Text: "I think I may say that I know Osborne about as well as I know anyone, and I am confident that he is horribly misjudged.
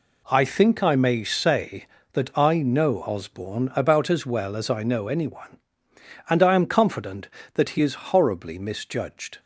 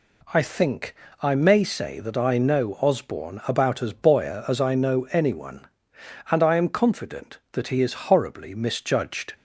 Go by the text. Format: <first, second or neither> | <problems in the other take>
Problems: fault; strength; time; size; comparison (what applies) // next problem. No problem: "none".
first | pauses between "think" and "I"; slight; at 0.9 s; 0.26 s long // says "boyer" for "well"; at 3.9 s